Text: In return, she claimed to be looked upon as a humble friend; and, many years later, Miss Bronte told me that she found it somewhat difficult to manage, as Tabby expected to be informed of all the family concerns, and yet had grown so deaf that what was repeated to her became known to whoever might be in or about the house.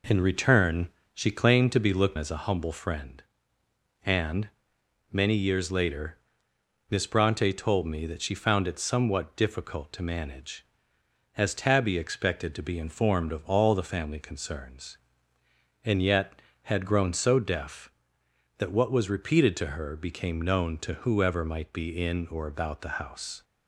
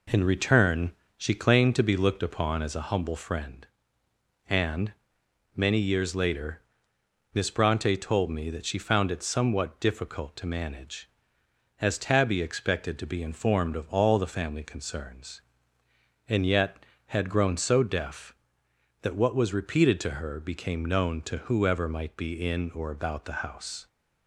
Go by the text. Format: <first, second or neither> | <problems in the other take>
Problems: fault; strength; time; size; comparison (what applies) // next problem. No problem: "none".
second | skips "upon"; at 2.1 s